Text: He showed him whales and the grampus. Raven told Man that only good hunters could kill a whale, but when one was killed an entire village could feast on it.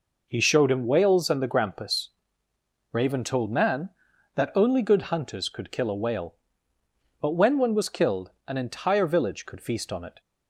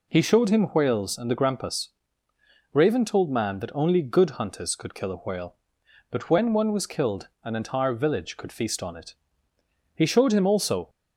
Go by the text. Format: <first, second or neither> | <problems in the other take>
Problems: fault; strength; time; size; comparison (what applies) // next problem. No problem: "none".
first | pauses between "killed" and "an"; slight; at 7.2 s; 0.16 s long; slight in the first // goes on to say "He showed him also"; noticeable; from 9.9 s on; 0.94 s long